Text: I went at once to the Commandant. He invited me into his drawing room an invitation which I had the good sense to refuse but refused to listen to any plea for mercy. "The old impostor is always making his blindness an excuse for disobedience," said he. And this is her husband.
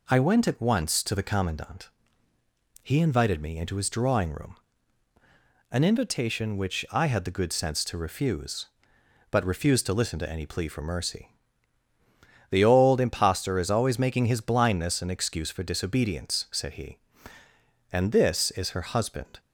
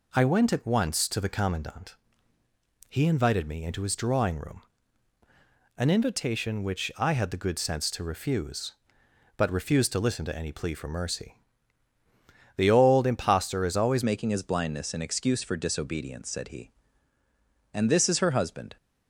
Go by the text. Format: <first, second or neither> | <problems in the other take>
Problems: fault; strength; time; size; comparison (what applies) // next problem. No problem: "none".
first | pauses between "room" and "an"; at 4.6 s; 1.1 s long; also in the first // changes voice at "making"; from 14.0 s on; 4.7 s long